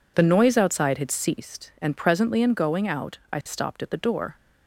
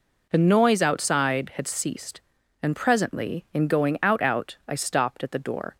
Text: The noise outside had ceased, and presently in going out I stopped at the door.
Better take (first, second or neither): first